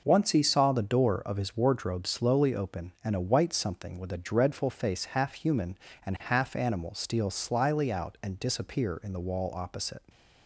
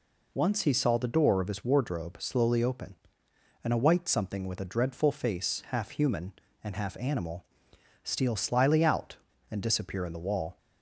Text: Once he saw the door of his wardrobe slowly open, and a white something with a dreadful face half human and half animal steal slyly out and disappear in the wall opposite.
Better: first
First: none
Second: pauses between "animal" and "steal"; noticeable; at 7.4 s; 0.58 s long // stops before "opposite"; at 10.5 s

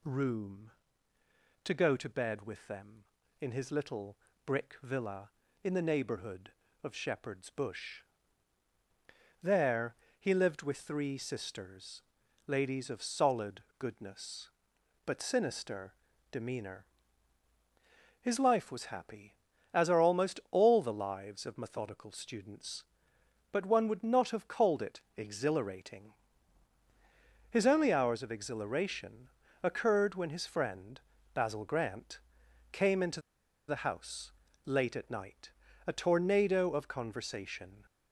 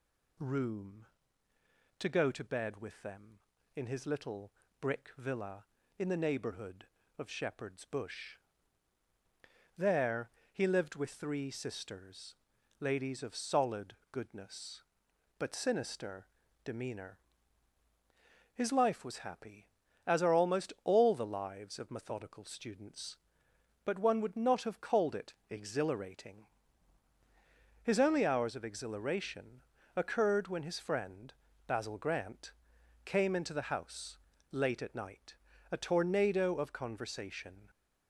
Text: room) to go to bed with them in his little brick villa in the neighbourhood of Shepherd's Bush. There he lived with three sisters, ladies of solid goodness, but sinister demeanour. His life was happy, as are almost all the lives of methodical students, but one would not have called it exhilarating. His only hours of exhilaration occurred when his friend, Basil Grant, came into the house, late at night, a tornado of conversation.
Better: second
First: pauses between "little" and "brick"; slight; at 4.1 s; 0.28 s long // pauses between "There" and "he"; slight; at 9.9 s; 0.24 s long // pauses between "solid" and "goodness"; slight; at 13.6 s; 0.18 s long // pauses between "sinister" and "demeanour"; at 15.9 s; 0.38 s long // pauses between "it" and "exhilarating"; slight; at 25.0 s; 0.16 s long // pauses between "exhilaration" and "occurred"; slight; at 29.2 s; 0.34 s long // pauses between "into" and "the"; noticeable; at 33.2 s; 0.47 s long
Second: pauses between "little" and "brick"; slight; at 4.5 s; 0.28 s long // pauses between "There" and "he"; slight; at 10.2 s; 0.24 s long // pauses between "solid" and "goodness"; slight; at 13.9 s; 0.18 s long // pauses between "sinister" and "demeanour"; at 16.2 s; 0.38 s long // pauses between "it" and "exhilarating"; slight; at 25.3 s; 0.16 s long // pauses between "exhilaration" and "occurred"; slight; at 29.6 s; 0.34 s long

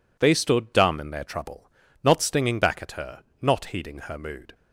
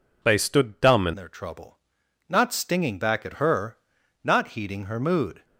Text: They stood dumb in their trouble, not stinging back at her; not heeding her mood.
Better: first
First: none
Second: changes voice at "their"; from 1.1 s on; 4.3 s long

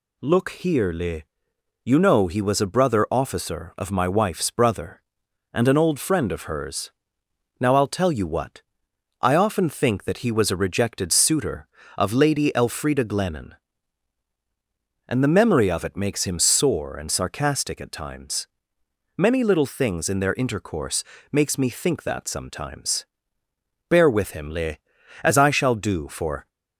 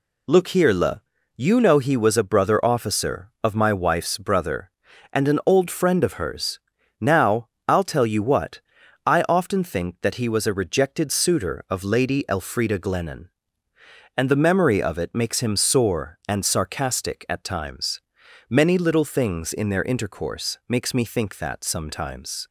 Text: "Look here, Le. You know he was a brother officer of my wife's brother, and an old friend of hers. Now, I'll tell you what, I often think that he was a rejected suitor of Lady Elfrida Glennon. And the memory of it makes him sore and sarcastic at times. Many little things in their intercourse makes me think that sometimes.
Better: second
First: pauses between "intercourse" and "makes"; slight; at 21.0 s; 0.26 s long // goes on to say "Bear with him Le as I shall do for"; strong; from 23.8 s on; 2.6 s long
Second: none

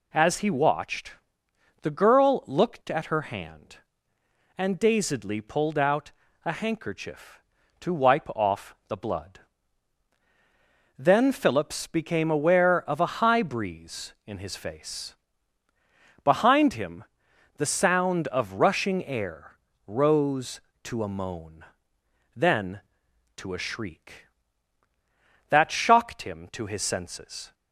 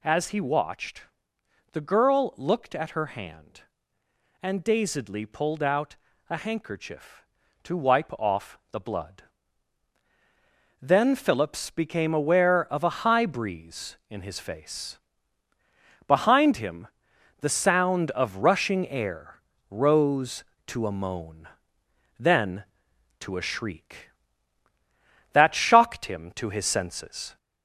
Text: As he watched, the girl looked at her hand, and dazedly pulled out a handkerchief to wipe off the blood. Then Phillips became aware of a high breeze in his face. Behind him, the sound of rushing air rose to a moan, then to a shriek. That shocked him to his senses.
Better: first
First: pauses between "out" and "a"; slight; at 6.1 s; 0.34 s long // pauses between "air" and "rose"; slight; at 19.5 s; 0.30 s long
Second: gets louder; slight; throughout; 2 dB // pauses between "out" and "a"; slight; at 5.9 s; 0.34 s long // pauses between "air" and "rose"; slight; at 19.4 s; 0.30 s long

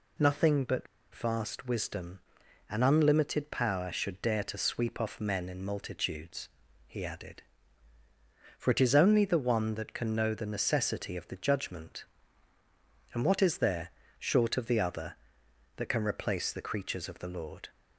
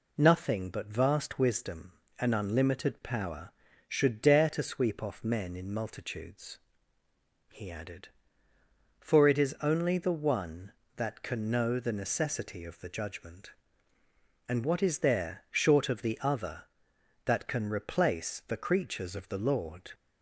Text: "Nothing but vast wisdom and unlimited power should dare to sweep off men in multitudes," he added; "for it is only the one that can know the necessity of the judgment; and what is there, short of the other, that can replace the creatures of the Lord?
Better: second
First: pauses between "but" and "vast"; slight; at 0.8 s; 0.28 s long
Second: none

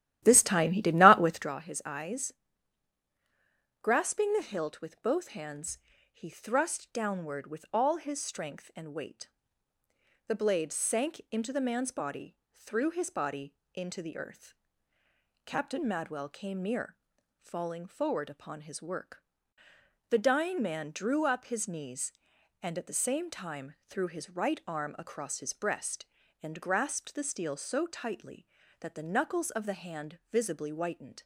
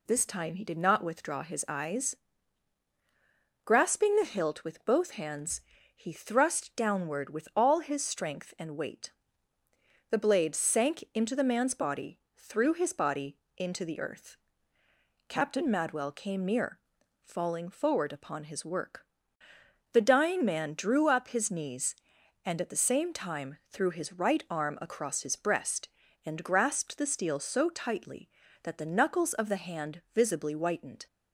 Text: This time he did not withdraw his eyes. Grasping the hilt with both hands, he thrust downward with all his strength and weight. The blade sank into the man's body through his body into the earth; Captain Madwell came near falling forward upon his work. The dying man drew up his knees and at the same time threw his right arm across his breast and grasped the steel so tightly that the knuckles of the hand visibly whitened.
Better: second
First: starts louder than the rest; strong; until 1.5 s; 13 dB // pauses between "body" and "through"; slight; at 12.3 s; 0.18 s long // pauses between "body" and "into"; slight; at 13.5 s; 0.20 s long // pauses between "near" and "falling"; at 16.9 s; 0.44 s long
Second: pauses between "body" and "through"; slight; at 12.1 s; 0.18 s long // pauses between "body" and "into"; slight; at 13.3 s; 0.20 s long // pauses between "near" and "falling"; at 16.7 s; 0.44 s long

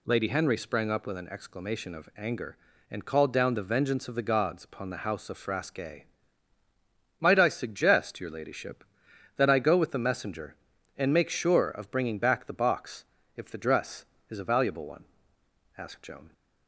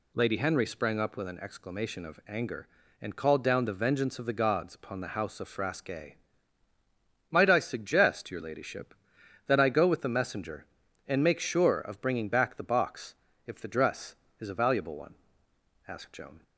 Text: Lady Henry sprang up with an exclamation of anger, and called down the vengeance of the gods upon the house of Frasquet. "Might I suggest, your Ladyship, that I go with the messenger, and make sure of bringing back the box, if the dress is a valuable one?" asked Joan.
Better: neither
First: none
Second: none

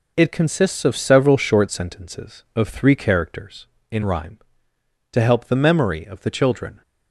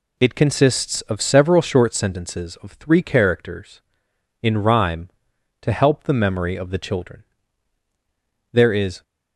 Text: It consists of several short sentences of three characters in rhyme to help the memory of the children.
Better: first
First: none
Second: goes on to say "There is"; from 8.5 s on; 0.50 s long

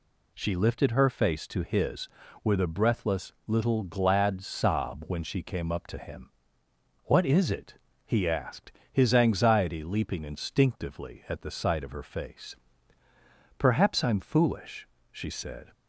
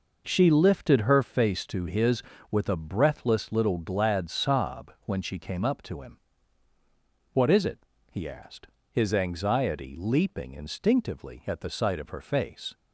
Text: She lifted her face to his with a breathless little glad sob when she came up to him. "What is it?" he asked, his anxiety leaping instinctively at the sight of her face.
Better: second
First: goes on to say "Perhaps I'm foolish she said"; strong; from 13.5 s on; 2.1 s long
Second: none

